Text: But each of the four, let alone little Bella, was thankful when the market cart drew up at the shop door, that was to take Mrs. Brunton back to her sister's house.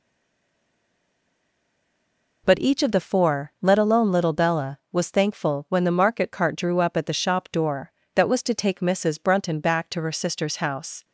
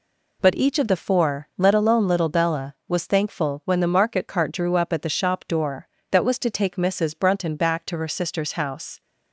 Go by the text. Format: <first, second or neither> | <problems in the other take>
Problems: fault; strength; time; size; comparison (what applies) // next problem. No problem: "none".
second | stays silent before the first word; until 2.4 s; 2.4 s long